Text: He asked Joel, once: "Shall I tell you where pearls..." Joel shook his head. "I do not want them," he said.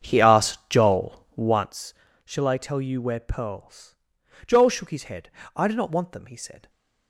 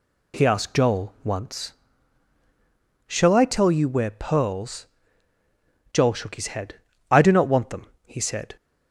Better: second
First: starts louder than the rest; strong; until 1.8 s; 7.5 dB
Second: none

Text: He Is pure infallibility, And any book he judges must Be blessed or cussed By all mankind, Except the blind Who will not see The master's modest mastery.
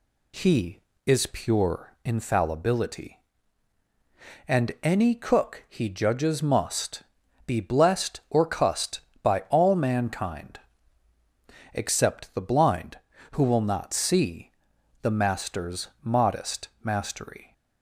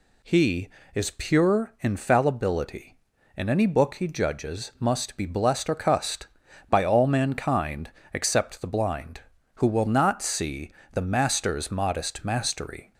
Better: second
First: says "cook" for "book"; at 5.1 s // pauses between "must" and "Be"; at 7.0 s; 0.44 s long // pauses between "see" and "The"; noticeable; at 14.5 s; 0.52 s long // pauses between "master's" and "modest"; slight; at 15.8 s; 0.16 s long // pauses between "modest" and "mastery"; slight; at 16.6 s; 0.16 s long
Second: pauses between "see" and "The"; slight; at 10.7 s; 0.22 s long

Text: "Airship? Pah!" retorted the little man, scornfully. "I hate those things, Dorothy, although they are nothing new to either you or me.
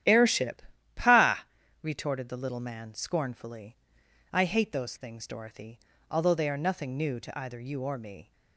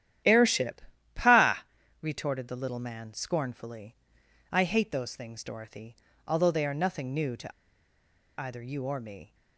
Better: first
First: starts louder than the rest; strong; until 1.4 s; 11 dB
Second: starts louder than the rest; strong; until 1.5 s; 11 dB // pauses between "to" and "either"; noticeable; at 7.5 s; 0.87 s long

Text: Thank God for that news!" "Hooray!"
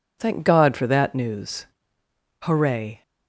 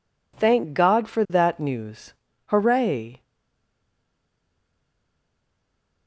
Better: first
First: none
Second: stays silent after the last word; strong; from 3.2 s on; 2.8 s long

